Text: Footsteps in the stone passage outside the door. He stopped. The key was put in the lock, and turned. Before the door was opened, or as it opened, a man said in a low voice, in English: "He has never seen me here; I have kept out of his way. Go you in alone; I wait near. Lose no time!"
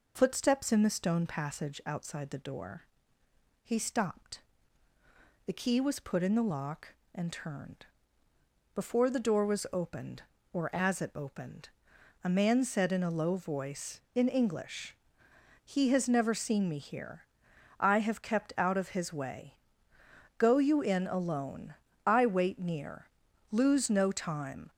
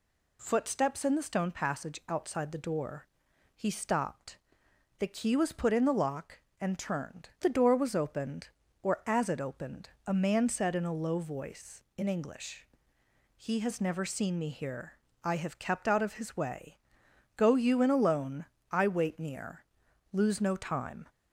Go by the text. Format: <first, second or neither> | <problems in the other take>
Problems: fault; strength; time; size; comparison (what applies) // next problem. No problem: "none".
first | skips "Before"; at 7.3 s